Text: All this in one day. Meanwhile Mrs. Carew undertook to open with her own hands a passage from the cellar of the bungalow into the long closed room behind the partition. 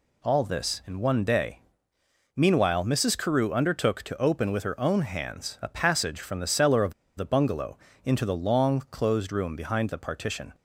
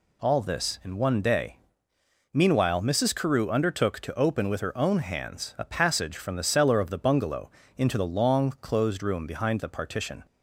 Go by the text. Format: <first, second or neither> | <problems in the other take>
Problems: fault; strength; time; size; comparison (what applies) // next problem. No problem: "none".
second | pauses between "of" and "the"; slight; at 6.9 s; 0.24 s long // pauses between "bungalow" and "into"; slight; at 7.7 s; 0.26 s long; slight in the second